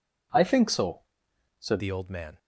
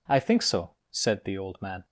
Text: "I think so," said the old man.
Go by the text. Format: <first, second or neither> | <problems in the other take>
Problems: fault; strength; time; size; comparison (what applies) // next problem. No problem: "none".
second | changes voice at "the"; from 1.7 s on; 0.6 s long